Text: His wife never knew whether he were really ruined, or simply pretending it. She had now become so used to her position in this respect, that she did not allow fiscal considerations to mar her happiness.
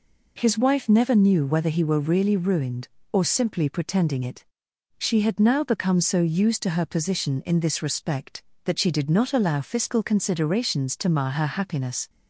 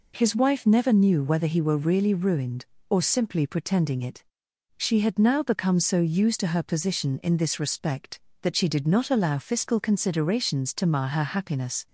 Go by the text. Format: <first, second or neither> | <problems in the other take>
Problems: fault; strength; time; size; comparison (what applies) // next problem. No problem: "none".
neither | none